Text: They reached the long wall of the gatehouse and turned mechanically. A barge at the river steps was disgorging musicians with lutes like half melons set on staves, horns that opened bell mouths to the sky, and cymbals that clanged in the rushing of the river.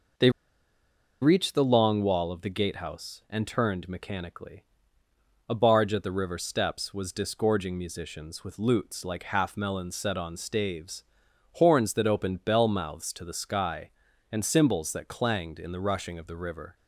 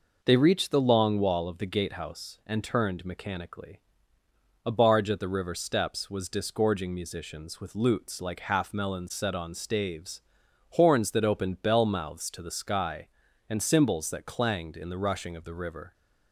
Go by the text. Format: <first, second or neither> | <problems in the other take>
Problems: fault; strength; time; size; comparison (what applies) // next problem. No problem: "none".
second | pauses between "They" and "reached"; noticeable; at 0.2 s; 0.91 s long